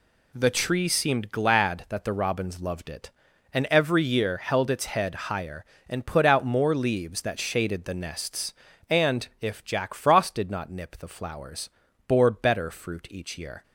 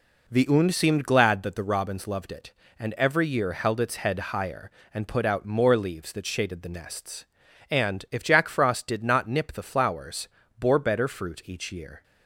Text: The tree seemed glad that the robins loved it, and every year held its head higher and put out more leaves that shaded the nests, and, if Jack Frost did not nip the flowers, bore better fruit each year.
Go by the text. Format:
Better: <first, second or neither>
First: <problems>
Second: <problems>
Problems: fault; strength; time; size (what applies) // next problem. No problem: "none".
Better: first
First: none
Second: says "und" for "tree"; at 0.4 s